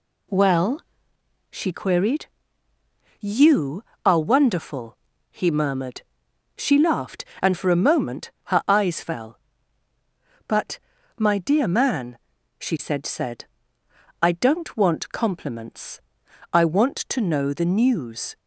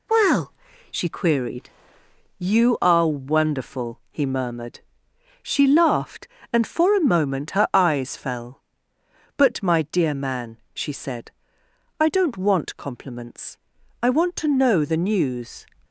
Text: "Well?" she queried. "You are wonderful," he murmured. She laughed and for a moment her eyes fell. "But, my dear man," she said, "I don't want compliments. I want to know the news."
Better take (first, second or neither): second